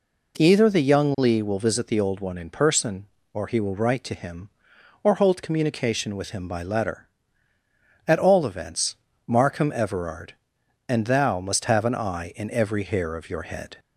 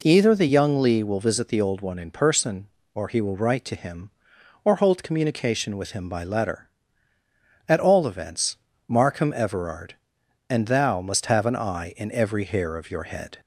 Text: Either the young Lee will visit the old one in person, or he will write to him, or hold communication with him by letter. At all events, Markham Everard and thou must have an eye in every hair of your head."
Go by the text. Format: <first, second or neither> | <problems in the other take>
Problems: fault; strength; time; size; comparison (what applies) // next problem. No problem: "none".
neither | none